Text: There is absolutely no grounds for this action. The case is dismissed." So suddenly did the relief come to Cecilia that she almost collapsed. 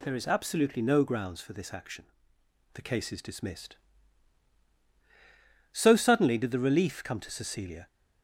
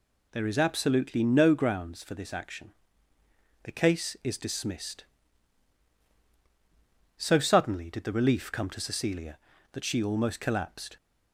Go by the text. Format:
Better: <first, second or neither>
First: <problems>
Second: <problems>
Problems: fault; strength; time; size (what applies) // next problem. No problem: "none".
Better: second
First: stops before "that she almost collapsed"; at 7.8 s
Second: none